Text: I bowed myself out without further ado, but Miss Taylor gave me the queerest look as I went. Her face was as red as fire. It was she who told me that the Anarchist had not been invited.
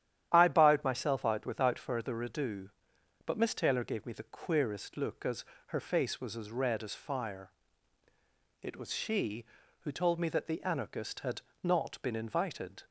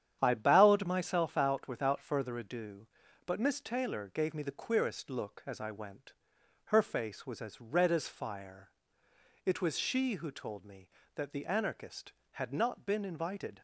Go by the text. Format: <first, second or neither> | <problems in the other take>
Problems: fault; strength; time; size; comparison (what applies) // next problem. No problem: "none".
second | starts louder than the rest; strong; until 1.3 s; 11 dB; strong in the second // skips "I went"; at 5.5 s // pauses between "had" and "not"; slight; at 11.4 s; 0.22 s long